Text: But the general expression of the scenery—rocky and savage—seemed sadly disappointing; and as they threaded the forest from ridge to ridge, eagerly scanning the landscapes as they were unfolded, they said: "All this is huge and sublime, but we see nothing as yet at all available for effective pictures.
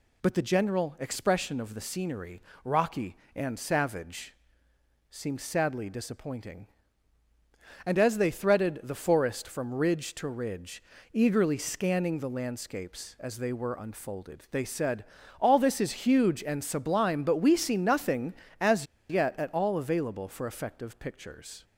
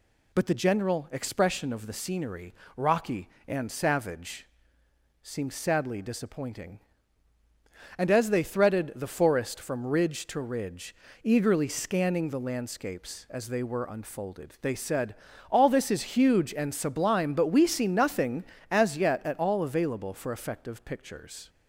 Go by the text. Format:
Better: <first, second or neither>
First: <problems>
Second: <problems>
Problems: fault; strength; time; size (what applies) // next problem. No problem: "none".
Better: second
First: pauses between "as" and "yet"; slight; at 18.8 s; 0.23 s long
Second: none